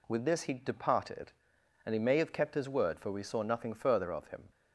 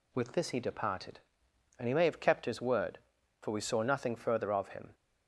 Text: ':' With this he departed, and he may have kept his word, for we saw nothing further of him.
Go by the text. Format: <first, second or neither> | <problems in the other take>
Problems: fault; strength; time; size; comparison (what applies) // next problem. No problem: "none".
neither | none